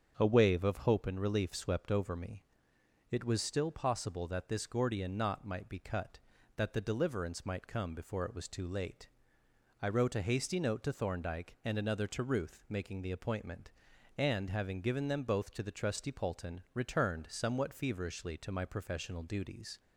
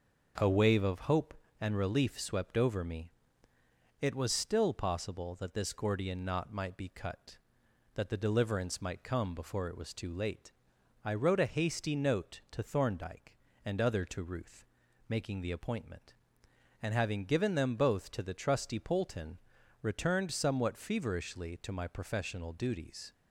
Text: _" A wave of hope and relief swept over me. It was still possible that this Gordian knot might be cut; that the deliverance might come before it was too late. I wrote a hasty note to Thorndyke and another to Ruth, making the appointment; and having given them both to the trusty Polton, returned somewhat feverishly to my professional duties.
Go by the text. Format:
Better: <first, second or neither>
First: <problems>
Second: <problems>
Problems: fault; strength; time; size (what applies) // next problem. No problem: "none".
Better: first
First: starts louder than the rest; strong; until 1.1 s; 7 dB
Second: starts louder than the rest; noticeable; until 1.6 s; 6 dB // says "other" for "another"; at 13.8 s